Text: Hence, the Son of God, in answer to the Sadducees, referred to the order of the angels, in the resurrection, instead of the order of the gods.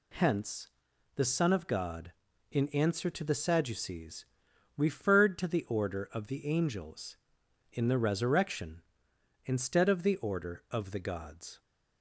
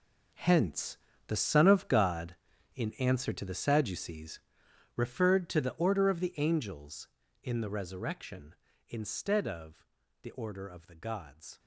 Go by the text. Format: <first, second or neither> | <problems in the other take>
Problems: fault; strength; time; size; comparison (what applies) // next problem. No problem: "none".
first | gets quieter; strong; throughout; 14 dB // pauses between "of" and "the"; slight; at 9.8 s; 0.36 s long